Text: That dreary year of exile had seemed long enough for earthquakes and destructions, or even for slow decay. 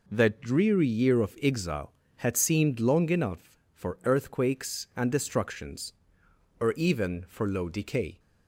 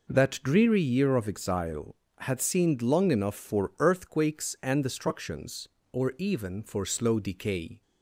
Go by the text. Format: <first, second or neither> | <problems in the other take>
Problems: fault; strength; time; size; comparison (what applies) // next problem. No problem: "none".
second | says "low" for "slow"; at 7.4 s